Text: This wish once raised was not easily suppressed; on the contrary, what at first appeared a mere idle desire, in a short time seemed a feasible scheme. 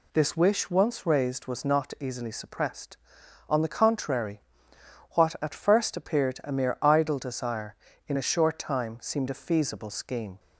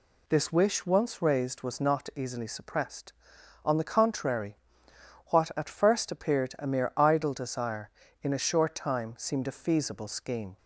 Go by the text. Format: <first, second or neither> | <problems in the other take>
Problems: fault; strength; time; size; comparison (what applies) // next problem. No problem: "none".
neither | none